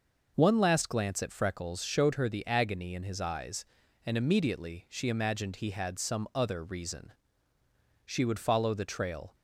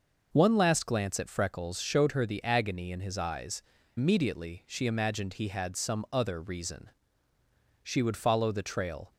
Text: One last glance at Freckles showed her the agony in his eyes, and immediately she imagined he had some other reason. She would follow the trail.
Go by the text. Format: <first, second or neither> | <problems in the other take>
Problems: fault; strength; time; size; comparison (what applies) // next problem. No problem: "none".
first | skips "and"; at 3.7 s